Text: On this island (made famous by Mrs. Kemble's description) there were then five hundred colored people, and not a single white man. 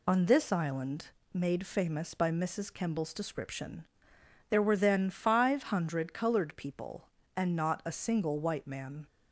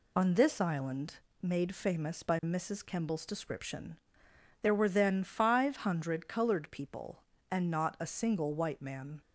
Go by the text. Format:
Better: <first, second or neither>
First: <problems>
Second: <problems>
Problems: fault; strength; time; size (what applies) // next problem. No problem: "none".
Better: neither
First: none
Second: none